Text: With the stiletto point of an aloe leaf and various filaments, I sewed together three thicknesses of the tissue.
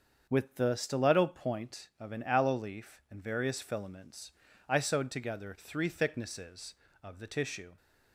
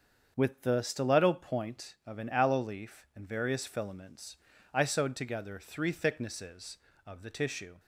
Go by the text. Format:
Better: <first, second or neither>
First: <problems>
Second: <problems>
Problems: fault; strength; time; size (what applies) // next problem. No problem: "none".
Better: neither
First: starts louder than the rest; until 1.3 s; 7 dB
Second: starts louder than the rest; until 1.3 s; 7 dB